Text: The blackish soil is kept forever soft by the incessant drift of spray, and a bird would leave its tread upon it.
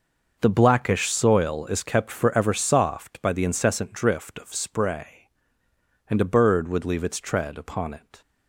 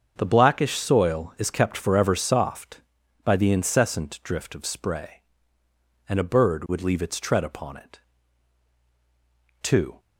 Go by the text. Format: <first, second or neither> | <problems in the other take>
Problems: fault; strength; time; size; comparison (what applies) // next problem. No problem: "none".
first | starts louder than the rest; until 1.1 s; 7 dB; noticeable in the first // goes on to say "Two"; slight; from 9.6 s on; 0.36 s long